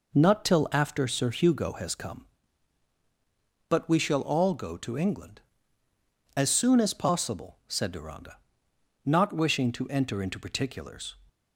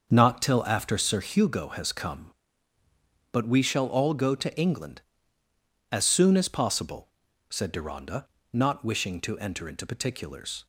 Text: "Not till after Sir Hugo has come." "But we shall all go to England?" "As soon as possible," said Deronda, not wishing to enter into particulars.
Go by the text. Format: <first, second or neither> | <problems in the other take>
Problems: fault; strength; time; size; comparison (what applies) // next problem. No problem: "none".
first | starts louder than the rest; until 1.4 s; 6.5 dB